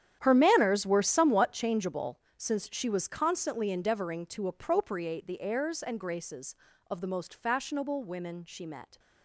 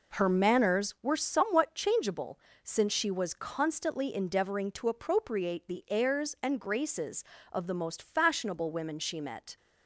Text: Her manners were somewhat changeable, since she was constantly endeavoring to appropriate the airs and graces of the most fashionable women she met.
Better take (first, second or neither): second